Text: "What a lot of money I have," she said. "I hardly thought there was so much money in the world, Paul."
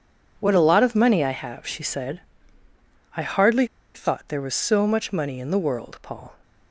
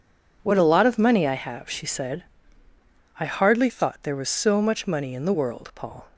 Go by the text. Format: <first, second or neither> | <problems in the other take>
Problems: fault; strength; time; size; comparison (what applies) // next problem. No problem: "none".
second | pauses between "hardly" and "thought"; slight; at 3.6 s; 0.28 s long